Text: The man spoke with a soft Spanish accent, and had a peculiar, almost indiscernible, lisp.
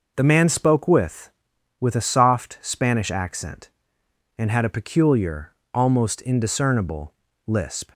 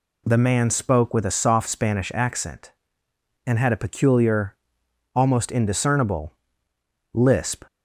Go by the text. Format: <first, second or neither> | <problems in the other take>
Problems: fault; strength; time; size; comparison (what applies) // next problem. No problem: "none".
second | says "with" twice; at 1.8 s